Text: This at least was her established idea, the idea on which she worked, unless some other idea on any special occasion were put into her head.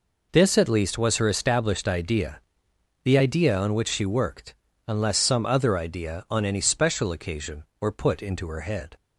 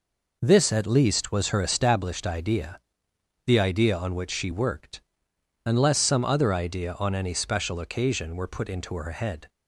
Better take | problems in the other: neither | none

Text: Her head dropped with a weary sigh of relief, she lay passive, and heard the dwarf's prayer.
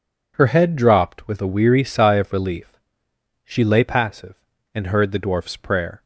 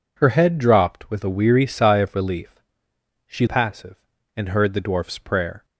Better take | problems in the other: first | skips "lay"; at 3.4 s

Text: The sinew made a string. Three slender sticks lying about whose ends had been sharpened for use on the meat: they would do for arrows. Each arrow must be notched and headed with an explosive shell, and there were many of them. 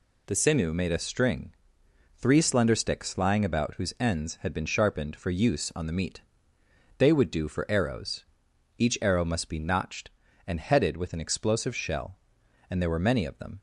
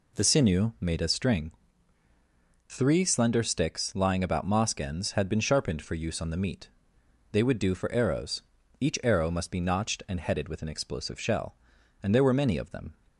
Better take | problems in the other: first | says "mosque" for "whose"; at 4.4 s

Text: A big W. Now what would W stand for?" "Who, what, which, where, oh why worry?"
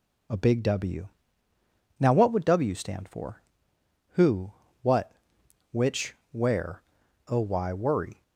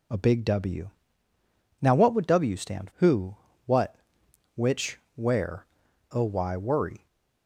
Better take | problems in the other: first | skips "for"; at 2.9 s

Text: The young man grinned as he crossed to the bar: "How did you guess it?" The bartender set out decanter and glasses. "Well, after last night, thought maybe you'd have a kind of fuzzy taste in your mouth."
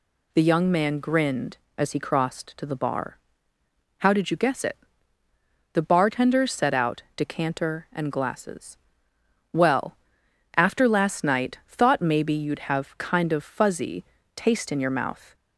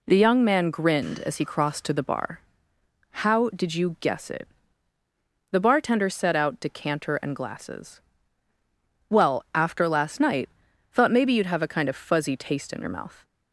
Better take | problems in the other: second | skips "a"; at 12.9 s // pauses between "fuzzy" and "taste"; slight; at 14.0 s; 0.32 s long

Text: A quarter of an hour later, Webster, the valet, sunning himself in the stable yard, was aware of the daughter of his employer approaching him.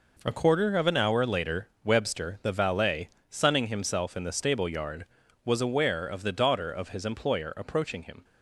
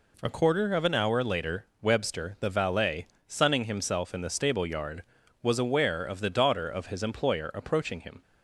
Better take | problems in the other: second | gets quieter; strong; throughout; 8.5 dB

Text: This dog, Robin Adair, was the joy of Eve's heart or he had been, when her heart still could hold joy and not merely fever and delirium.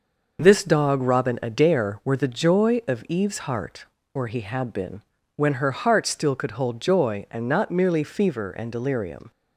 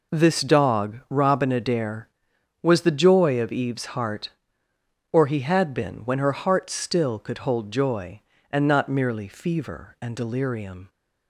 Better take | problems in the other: second | says "were" for "was"; at 2.0 s

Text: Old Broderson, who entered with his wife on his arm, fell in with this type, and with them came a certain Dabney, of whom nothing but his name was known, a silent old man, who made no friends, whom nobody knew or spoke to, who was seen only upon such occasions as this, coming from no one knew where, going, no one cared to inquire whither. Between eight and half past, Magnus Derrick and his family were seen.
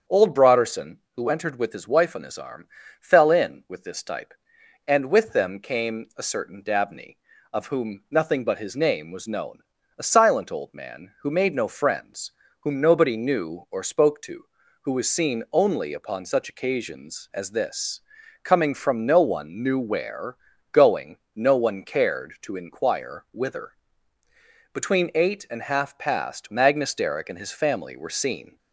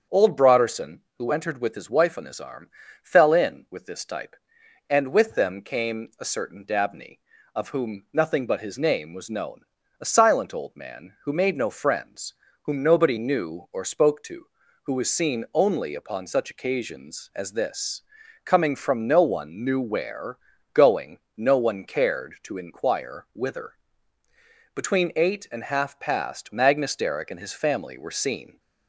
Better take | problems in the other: neither | starts louder than the rest; strong; the same in both

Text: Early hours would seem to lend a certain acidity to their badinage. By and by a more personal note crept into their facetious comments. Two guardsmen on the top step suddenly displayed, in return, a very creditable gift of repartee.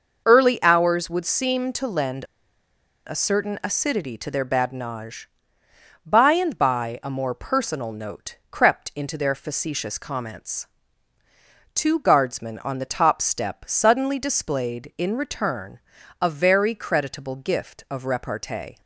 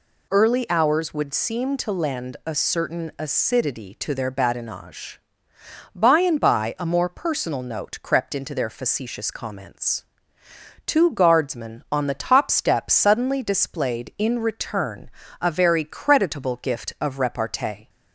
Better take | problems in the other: second | pauses between "lend" and "a"; noticeable; at 2.2 s; 0.82 s long

